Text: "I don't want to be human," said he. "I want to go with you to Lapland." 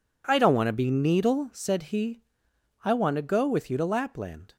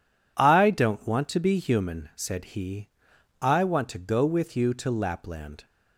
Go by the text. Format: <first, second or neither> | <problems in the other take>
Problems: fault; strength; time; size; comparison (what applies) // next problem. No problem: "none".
second | says "needle" for "human"; at 0.8 s